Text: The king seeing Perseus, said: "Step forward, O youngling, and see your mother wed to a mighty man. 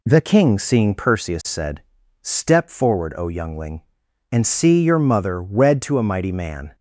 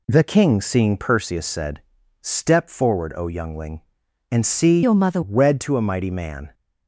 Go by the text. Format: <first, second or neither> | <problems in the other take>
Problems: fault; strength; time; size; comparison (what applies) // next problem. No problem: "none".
first | changes voice from "your" to "mother"; from 4.8 to 5.2 s; 0.4 s long